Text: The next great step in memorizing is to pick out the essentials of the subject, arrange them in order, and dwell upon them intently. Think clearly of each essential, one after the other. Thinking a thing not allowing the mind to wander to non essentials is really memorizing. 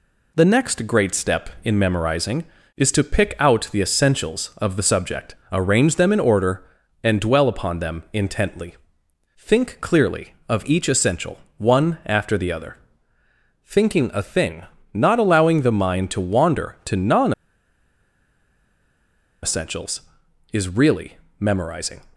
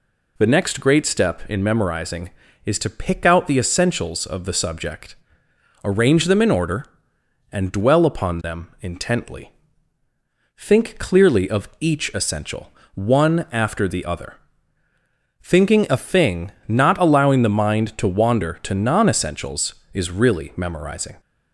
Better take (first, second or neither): second